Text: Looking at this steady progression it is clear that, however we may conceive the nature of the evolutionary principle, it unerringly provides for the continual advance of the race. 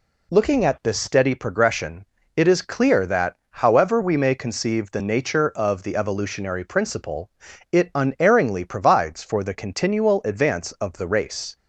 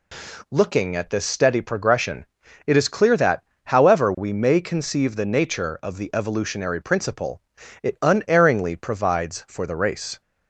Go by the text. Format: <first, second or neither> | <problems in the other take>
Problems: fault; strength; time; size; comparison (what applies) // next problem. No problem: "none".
first | pauses between "progression" and "it"; at 2.2 s; 0.40 s long; slight in the first // skips "the continual advance of"; at 9.6 s